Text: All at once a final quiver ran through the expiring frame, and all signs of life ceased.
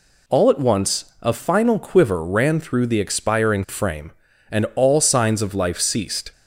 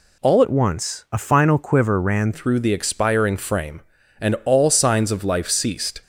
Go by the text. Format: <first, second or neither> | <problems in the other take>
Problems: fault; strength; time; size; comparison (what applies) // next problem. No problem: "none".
first | changes voice from "at" to "ran"; from 0.4 to 2.3 s; 1.9 s long